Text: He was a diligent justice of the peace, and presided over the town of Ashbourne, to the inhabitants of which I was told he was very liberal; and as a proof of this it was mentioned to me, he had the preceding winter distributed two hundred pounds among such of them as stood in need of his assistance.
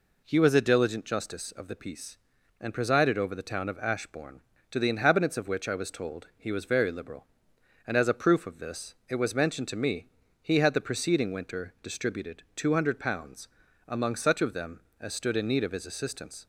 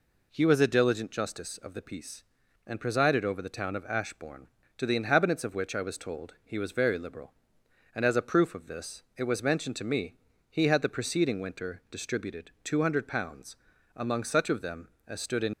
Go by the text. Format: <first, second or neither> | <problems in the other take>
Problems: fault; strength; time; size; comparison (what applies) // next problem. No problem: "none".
first | pauses between "pounds" and "among"; at 13.5 s; 0.40 s long; also in the first // stops before "need of his assistance"; at 15.5 s